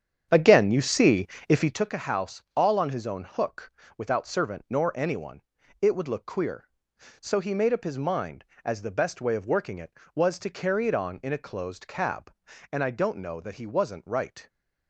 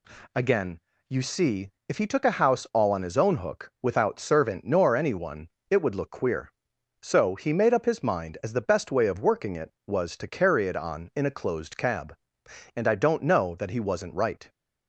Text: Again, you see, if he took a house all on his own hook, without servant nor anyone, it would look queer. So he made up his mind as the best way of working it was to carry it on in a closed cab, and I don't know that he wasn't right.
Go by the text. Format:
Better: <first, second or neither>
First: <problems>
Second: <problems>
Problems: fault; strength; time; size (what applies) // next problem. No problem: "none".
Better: second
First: starts louder than the rest; strong; until 1.9 s; 8.5 dB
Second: none